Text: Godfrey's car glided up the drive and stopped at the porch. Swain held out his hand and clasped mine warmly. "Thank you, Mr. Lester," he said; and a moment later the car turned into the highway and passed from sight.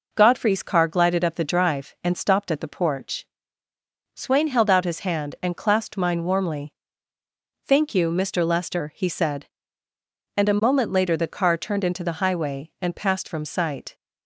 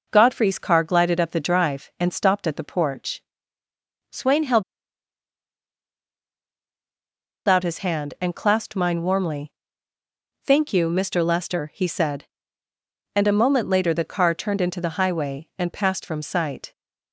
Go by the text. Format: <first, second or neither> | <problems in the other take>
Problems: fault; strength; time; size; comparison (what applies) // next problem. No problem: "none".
first | pauses between "held" and "out"; strong; at 4.6 s; 2.8 s long